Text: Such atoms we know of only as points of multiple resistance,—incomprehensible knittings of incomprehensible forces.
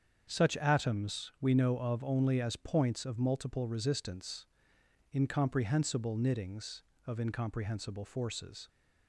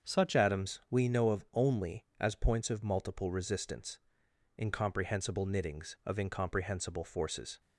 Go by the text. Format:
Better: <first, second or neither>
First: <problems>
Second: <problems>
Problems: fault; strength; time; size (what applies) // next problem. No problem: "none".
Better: first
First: starts louder than the rest; strong; until 1.3 s; 7.5 dB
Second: starts louder than the rest; until 1.1 s; 6.5 dB // changes voice at "atoms"; from 0.3 s on; 7.3 s long